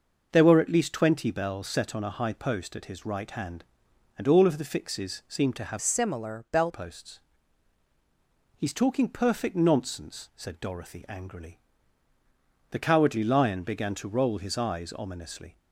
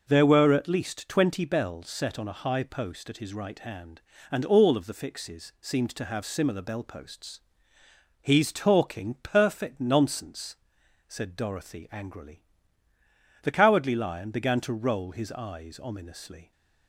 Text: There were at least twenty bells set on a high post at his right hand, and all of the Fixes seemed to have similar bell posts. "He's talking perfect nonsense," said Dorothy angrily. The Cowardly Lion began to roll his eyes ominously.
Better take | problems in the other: second | changes voice from "similar" to "bell"; from 5.8 to 6.7 s; 0.9 s long

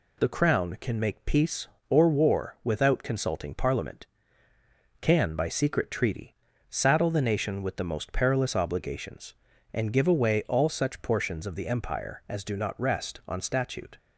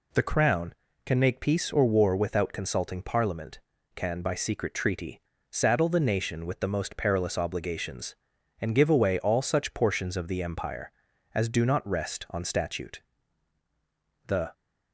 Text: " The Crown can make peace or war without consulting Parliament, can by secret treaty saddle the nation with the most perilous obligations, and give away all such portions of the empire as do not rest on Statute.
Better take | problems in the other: first | pauses between "treaty" and "saddle"; slight; at 5.2 s; 0.30 s long; slight in the first // goes on to say "The"; slight; from 14.2 s on; 0.24 s long

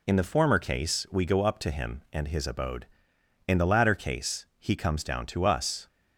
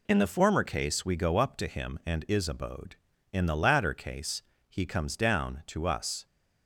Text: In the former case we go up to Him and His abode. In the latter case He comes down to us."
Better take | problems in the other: first | says "Is" for "His"; at 2.2 s // pauses between "case" and "He"; slight; at 4.4 s; 0.26 s long

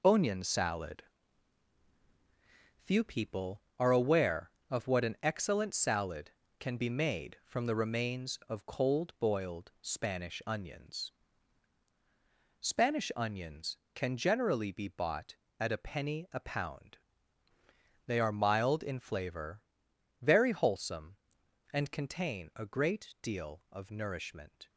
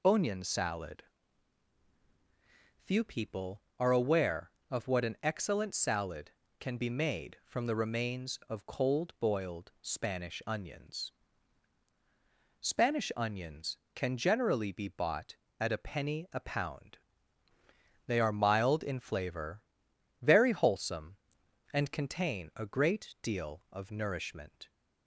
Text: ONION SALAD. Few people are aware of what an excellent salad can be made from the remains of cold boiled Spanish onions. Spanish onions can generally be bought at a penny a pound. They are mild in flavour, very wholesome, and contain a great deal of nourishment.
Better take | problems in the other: second | gets quieter; strong; throughout; 7.5 dB

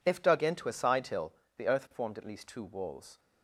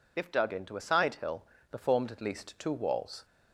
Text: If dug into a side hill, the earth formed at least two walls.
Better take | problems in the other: first | skips "earth"; at 1.7 s

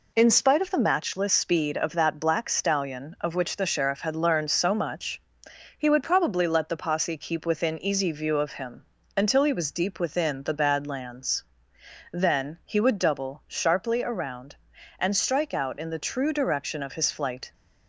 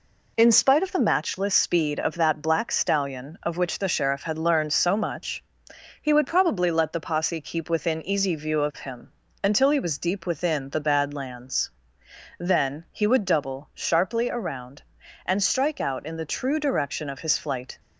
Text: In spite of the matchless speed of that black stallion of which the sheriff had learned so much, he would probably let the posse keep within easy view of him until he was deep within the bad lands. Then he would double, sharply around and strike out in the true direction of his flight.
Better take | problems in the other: neither | pauses between "him" and "until"; slight; the same in both

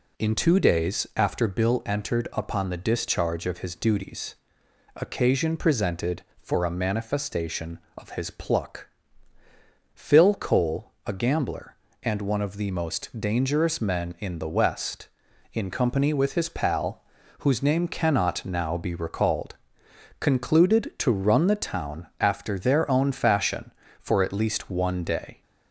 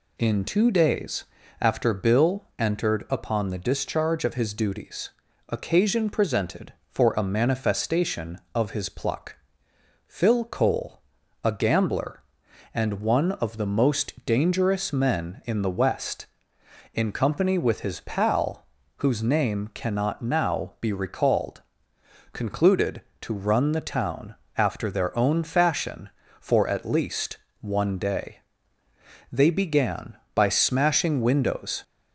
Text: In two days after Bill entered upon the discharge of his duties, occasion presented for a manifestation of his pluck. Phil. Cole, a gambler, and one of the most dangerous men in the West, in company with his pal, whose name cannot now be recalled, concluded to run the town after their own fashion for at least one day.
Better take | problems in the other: first | pauses between "days" and "after"; slight; at 1.2 s; 0.36 s long // pauses between "town" and "after"; slight; at 24.3 s; 0.24 s long // pauses between "least" and "one"; slight; at 27.3 s; 0.24 s long // goes on to say "They began by smashing windows"; strong; from 29.3 s on; 2.5 s long

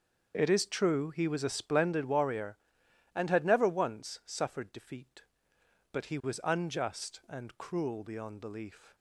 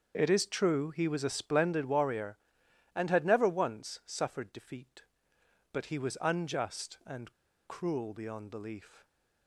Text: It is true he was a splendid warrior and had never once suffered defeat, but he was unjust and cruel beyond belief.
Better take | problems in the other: first | starts louder than the rest; until 1.1 s; 6.5 dB; also in the first // pauses between "and" and "cruel"; slight; at 7.3 s; 0.33 s long

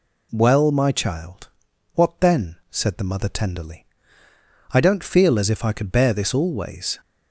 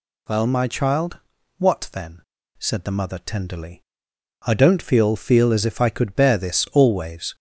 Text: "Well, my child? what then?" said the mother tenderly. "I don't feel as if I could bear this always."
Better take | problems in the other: first | says "feel" twice; at 5.1 s

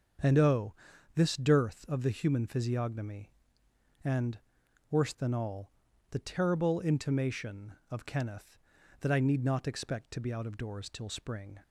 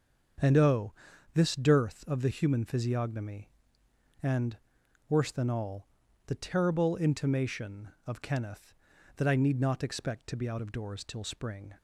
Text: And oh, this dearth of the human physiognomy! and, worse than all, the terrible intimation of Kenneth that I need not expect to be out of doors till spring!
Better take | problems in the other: neither | starts louder than the rest; the same in both

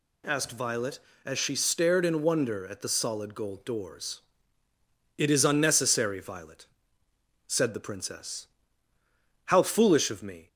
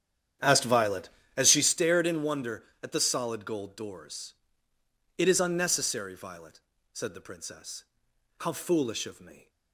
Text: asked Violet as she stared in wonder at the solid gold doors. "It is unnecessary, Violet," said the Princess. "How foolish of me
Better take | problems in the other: first | starts louder than the rest; strong; until 1.7 s; 9.5 dB

